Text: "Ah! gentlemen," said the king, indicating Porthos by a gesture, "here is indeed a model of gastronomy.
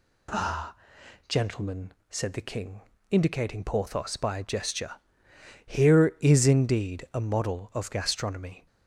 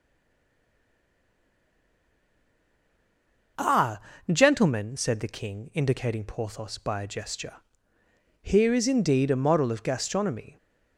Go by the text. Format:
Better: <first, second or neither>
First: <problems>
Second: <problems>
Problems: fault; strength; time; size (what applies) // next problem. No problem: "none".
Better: first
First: none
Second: stays silent before the first word; strong; until 3.5 s; 3.5 s long